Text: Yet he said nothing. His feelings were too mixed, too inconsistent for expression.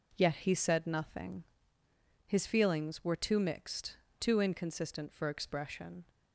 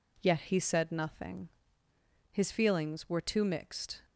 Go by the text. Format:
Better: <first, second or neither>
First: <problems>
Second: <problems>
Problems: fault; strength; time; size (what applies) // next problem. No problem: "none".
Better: first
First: none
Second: stops before "too inconsistent for expression"; at 4.0 s